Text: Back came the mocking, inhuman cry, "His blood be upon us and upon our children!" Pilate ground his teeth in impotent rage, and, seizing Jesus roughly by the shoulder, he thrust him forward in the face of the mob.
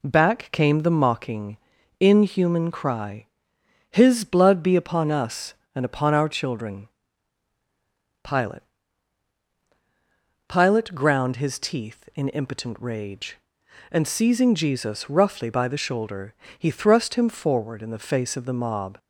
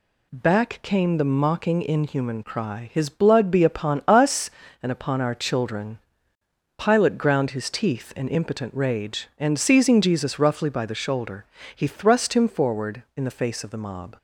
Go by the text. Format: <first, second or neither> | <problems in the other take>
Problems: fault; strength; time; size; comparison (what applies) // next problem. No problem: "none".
second | says "Pilate" twice; at 10.4 s